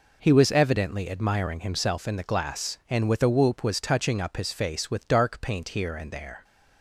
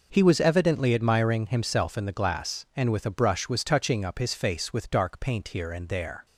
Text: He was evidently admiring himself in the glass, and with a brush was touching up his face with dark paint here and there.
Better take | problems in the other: second | says "whoop" for "brush"; at 3.2 s

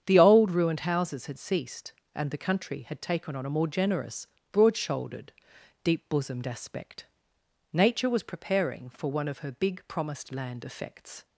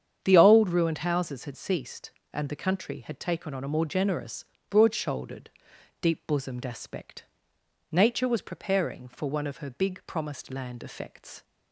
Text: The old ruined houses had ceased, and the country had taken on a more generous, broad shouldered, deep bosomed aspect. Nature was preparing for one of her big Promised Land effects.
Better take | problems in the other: neither | starts louder than the rest; strong; the same in both

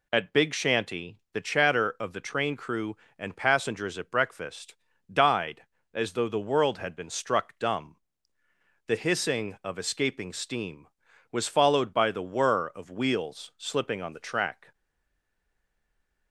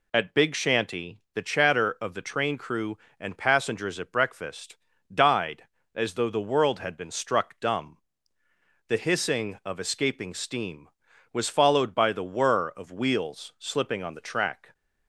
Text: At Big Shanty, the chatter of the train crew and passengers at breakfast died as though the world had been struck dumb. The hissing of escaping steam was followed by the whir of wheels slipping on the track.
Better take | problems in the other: second | pauses between "breakfast" and "died"; at 4.7 s; 0.38 s long; also in the second // stays silent after the last word; noticeable; from 14.7 s on; 1.6 s long

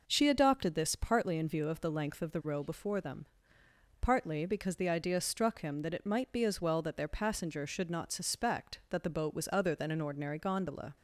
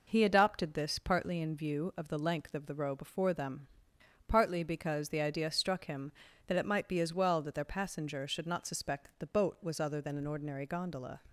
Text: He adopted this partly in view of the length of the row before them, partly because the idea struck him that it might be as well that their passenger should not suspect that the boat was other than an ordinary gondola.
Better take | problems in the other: second | says "She" for "He"; at 0.0 s

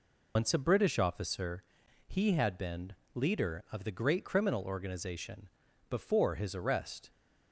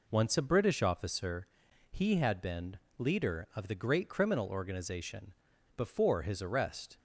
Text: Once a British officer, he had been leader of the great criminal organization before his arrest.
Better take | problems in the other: second | loses the start of "Once"; at 0.3 s; 100 ms // pauses between "been" and "leader"; slight; at 2.9 s; 0.20 s long; slight in the second // pauses between "organization" and "before"; at 5.4 s; 0.40 s long; also in the second

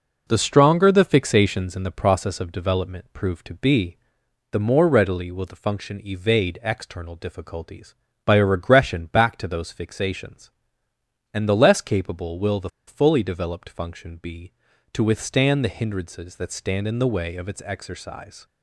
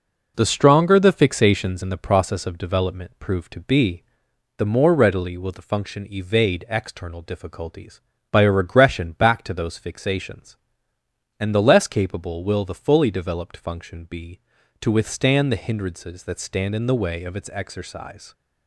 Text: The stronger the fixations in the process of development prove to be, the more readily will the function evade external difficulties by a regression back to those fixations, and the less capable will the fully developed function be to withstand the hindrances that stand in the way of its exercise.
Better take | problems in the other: second | pauses between "the" and "fully"; slight; at 12.6 s; 0.19 s long

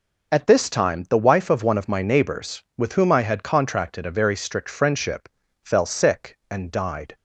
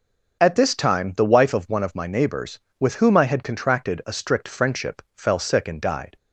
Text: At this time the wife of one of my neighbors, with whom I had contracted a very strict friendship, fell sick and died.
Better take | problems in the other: first | skips "very"; at 4.1 s

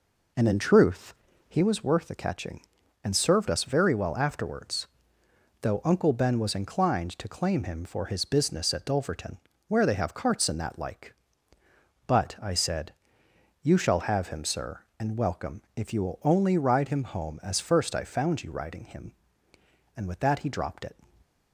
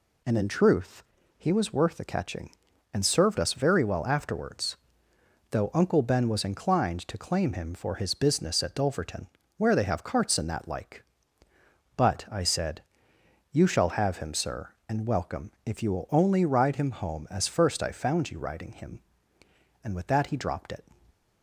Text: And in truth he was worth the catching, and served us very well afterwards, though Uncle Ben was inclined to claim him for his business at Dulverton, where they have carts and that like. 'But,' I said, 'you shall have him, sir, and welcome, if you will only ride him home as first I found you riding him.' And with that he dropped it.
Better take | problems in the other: second | starts louder than the rest; noticeable; until 1.7 s; 4.5 dB // pauses between "truth" and "he"; slight; at 1.1 s; 0.34 s long; slight in the second // stays silent after the last word; slight; from 21.0 s on; 0.5 s long

